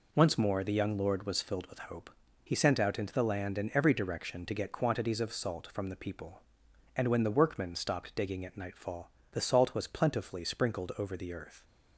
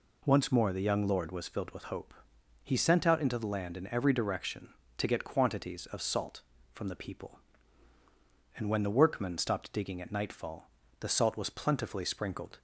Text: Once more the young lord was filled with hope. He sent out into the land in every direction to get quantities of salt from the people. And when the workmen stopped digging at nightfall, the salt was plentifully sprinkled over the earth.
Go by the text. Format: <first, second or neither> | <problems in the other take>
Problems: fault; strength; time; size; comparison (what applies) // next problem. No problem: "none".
first | stops before "over the earth"; at 12.5 s